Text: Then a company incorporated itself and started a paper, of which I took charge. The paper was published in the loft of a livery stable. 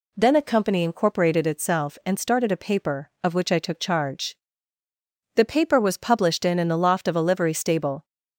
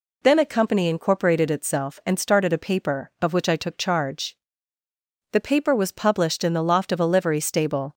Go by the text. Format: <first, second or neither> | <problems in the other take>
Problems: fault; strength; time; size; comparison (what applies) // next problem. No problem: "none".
second | says "in" twice; at 6.5 s